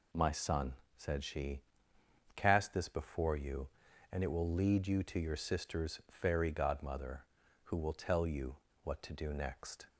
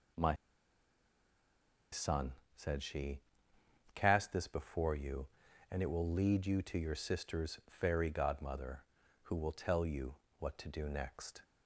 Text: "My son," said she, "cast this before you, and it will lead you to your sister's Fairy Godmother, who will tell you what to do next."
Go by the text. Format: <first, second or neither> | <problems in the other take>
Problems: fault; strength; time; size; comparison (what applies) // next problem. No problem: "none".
first | pauses between "My" and "son"; strong; at 0.3 s; 1.5 s long // pauses between "you" and "what"; slight; at 10.1 s; 0.24 s long; slight in the first